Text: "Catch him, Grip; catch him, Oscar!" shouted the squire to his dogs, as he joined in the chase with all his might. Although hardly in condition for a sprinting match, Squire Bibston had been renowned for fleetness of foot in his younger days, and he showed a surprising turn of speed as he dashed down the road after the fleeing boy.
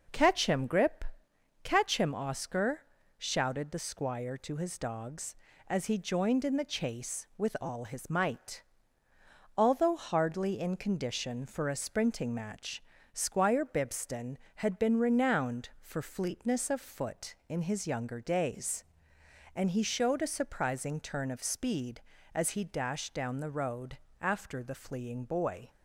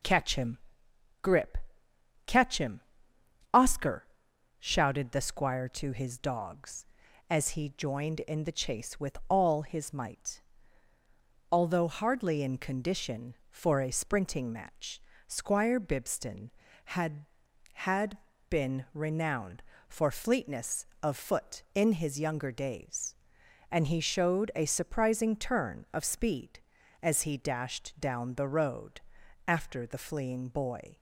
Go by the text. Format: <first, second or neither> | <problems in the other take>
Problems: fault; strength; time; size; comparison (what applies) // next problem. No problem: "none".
first | says "had" twice; at 17.7 s // pauses between "road" and "after"; at 29.0 s; 0.44 s long; slight in the first